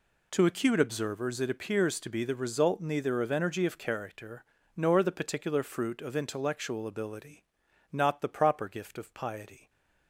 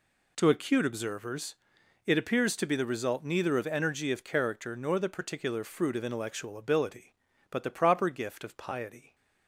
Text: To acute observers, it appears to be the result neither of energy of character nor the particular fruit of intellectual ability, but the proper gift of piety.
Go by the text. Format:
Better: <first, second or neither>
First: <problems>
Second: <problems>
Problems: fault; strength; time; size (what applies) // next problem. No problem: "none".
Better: second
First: pauses between "character" and "nor"; slight; at 4.4 s; 0.32 s long // says "not" for "but"; at 7.9 s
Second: none